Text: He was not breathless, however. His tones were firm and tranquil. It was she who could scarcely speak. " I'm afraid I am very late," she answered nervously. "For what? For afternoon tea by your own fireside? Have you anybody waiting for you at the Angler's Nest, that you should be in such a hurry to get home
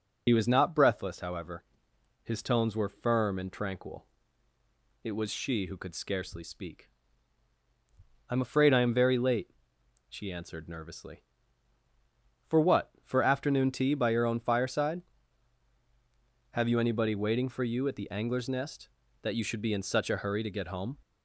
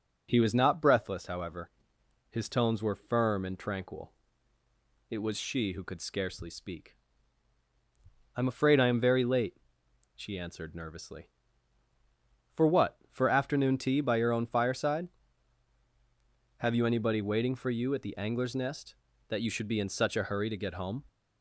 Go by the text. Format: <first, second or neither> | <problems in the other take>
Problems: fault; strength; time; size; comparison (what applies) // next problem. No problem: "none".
second | loses the start of "He"; at 0.2 s; 50 ms // starts louder than the rest; until 1.2 s; 6.5 dB; also in the second